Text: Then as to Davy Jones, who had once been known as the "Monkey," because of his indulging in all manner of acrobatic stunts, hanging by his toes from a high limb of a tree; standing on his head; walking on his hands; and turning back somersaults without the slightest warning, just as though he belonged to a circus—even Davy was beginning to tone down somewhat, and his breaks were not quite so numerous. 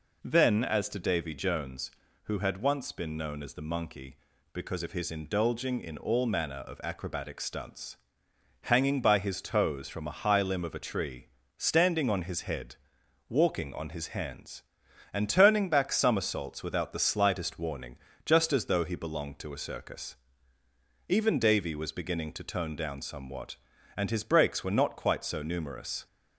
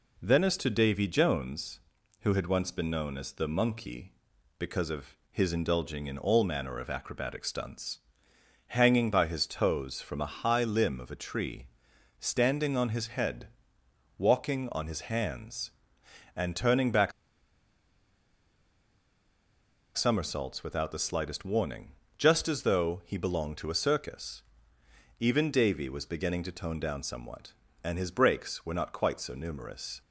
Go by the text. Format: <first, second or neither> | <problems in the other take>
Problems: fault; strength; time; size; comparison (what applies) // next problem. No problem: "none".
first | pauses between "of" and "his"; slight; at 5.1 s; 0.16 s long // pauses between "back" and "somersaults"; strong; at 17.1 s; 2.8 s long